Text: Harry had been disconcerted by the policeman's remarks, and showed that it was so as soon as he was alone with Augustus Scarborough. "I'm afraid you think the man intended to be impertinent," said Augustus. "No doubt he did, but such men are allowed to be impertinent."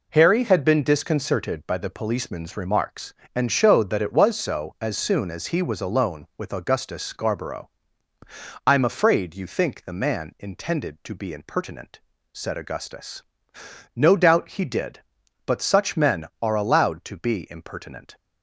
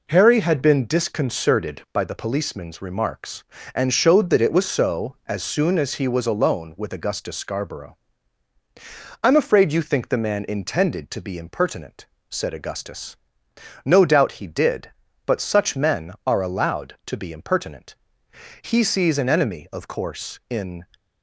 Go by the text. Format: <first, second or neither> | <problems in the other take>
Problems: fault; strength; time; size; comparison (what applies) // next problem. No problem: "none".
first | goes on to say "He sees an enemy of course in"; strong; from 18.6 s on; 2.2 s long